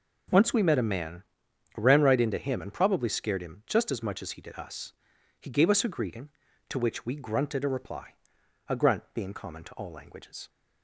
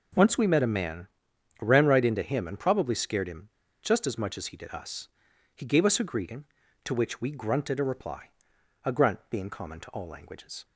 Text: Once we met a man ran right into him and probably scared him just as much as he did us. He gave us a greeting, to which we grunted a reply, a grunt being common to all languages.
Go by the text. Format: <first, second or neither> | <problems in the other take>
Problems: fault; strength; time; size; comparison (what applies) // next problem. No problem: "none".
first | pauses between "man" and "ran"; noticeable; at 1.0 s; 0.52 s long; noticeable in the first // pauses between "him" and "just"; slight; at 3.4 s; 0.33 s long